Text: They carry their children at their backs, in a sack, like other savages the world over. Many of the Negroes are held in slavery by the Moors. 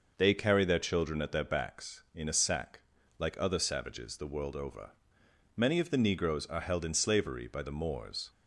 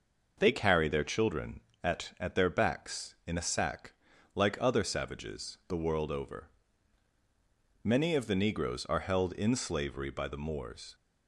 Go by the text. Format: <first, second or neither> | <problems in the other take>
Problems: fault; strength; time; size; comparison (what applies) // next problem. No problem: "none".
first | says "at" twice; at 2.2 s